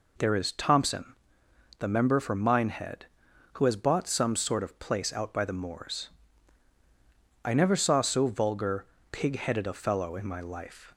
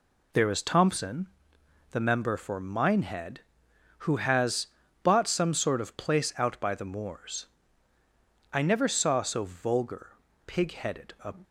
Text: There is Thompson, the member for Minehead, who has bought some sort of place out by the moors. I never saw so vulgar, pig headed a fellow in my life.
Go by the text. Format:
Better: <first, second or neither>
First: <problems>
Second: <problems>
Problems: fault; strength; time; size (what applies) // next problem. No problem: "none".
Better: first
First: none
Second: pauses between "has" and "bought"; slight; at 4.6 s; 0.36 s long // stops before "fellow in my life"; at 11.4 s